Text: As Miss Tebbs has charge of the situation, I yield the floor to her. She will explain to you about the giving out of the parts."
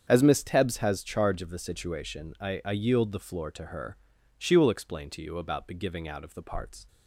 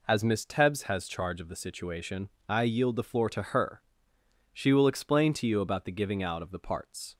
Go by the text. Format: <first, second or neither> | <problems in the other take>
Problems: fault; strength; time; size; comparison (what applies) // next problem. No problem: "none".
second | starts louder than the rest; strong; until 1.0 s; 7.5 dB // says "I" twice; at 2.6 s